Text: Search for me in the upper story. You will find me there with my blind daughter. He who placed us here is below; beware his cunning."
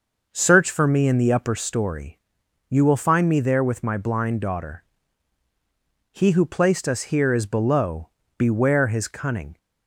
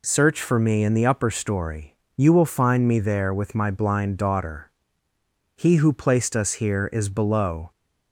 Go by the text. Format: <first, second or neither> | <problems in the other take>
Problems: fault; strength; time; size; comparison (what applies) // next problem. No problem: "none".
first | stops before "beware his cunning"; at 7.7 s